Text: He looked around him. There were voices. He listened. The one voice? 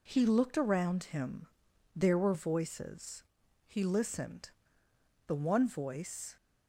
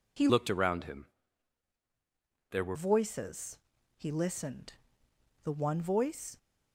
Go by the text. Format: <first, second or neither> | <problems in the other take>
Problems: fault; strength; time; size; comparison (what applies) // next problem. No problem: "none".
first | changes voice from "looked" to "were"; from 0.2 to 2.7 s; 2.5 s long